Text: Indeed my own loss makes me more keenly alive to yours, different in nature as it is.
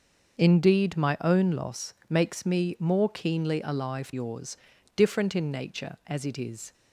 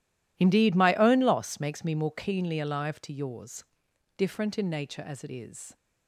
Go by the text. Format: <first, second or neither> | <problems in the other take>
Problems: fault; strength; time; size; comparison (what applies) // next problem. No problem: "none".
second | starts louder than the rest; until 1.4 s; 6.5 dB // pauses between "loss" and "makes"; slight; at 1.9 s; 0.16 s long // skips "to"; at 4.1 s